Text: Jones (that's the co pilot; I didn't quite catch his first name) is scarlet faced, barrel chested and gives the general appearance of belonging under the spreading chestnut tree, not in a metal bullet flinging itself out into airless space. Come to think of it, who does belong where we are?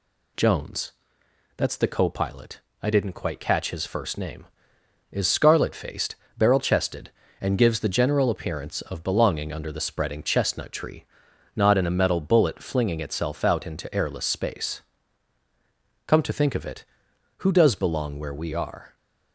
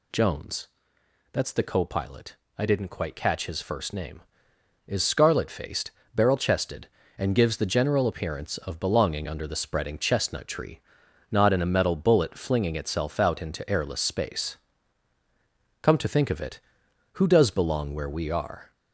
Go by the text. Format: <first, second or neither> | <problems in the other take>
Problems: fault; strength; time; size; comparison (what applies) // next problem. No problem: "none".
first | gets louder; throughout; 3.5 dB